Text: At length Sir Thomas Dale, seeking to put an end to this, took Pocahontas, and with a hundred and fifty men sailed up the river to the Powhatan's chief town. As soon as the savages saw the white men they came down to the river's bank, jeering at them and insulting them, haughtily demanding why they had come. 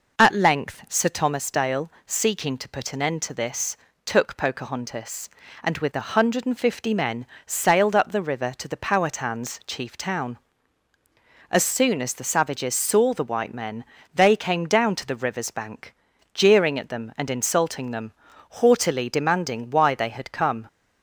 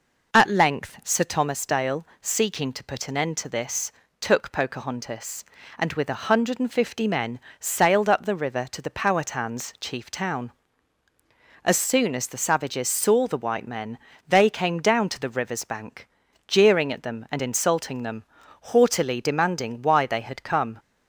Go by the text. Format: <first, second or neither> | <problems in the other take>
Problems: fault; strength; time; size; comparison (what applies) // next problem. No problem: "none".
neither | pauses between "men" and "sailed"; slight; the same in both // pauses between "men" and "they"; slight; the same in both